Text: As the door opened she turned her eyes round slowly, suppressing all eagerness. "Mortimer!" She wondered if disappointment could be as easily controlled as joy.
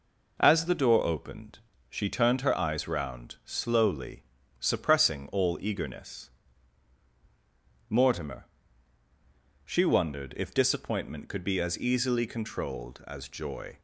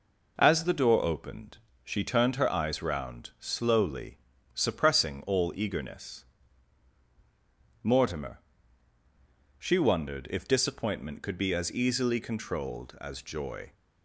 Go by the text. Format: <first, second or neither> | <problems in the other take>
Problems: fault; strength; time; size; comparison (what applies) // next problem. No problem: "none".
neither | pauses between "opened" and "she"; slight; the same in both